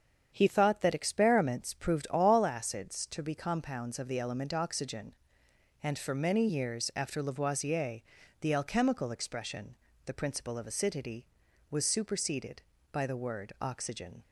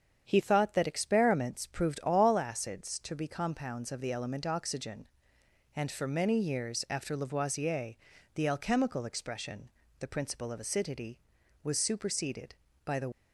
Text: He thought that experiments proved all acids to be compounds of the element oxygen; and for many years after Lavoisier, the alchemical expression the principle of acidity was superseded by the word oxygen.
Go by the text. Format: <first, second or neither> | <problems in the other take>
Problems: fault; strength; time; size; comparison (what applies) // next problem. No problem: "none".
first | starts louder than the rest; strong; until 1.2 s; 7.5 dB; strong in the first // pauses between "expression" and "the"; slight; at 9.6 s; 0.32 s long; slight in the first // stops before "word oxygen"; at 13.1 s